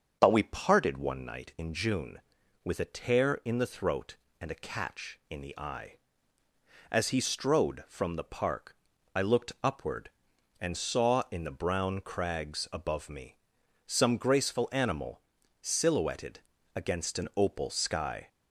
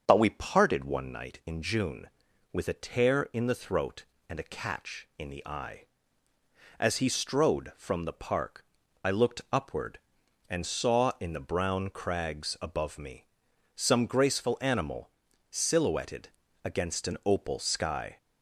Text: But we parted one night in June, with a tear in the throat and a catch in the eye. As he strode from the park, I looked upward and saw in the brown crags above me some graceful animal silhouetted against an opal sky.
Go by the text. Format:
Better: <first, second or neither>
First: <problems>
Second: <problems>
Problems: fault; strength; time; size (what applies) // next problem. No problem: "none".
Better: neither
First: starts louder than the rest; until 1.2 s; 6.5 dB // pauses between "me" and "some"; noticeable; at 13.3 s; 0.50 s long // pauses between "animal" and "silhouetted"; at 15.1 s; 0.42 s long // pauses between "silhouetted" and "against"; slight; at 16.3 s; 0.34 s long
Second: starts louder than the rest; until 1.0 s; 6.5 dB // pauses between "me" and "some"; noticeable; at 13.2 s; 0.50 s long // pauses between "animal" and "silhouetted"; at 15.0 s; 0.42 s long // pauses between "silhouetted" and "against"; slight; at 16.2 s; 0.34 s long